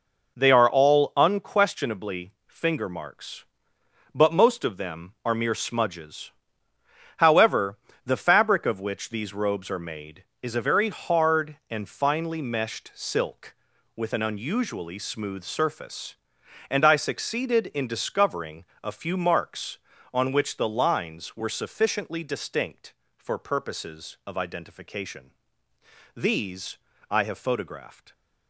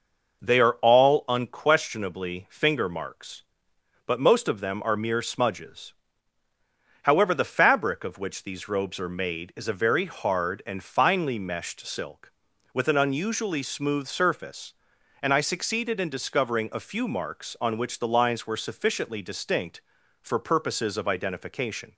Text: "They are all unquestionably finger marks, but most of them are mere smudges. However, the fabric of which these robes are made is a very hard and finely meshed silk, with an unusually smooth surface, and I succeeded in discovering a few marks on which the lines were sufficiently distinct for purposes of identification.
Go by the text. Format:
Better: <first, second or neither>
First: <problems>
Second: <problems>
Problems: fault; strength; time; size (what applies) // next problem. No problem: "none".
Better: second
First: pauses between "unquestionably" and "finger"; slight; at 2.3 s; 0.16 s long // pauses between "discovering" and "a"; slight; at 18.6 s; 0.18 s long // goes on to say "These I have photographed"; strong; from 26.1 s on; 1.9 s long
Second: none